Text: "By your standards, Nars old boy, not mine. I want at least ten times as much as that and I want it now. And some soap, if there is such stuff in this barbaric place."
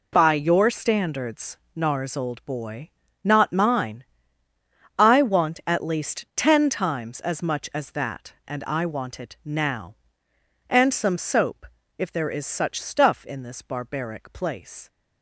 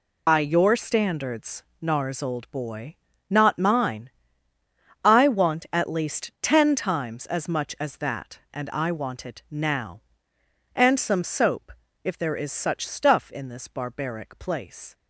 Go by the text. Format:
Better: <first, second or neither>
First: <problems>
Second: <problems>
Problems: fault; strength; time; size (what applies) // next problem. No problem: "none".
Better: first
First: none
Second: loses the start of "By"; at 0.2 s; 80 ms